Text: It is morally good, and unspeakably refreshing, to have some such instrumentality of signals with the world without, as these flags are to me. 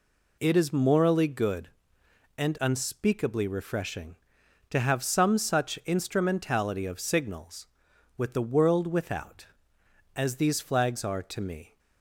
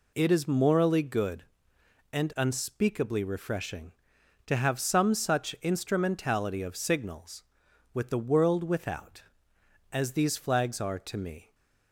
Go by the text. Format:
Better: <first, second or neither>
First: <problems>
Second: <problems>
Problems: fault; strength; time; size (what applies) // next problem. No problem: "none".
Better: neither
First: none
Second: none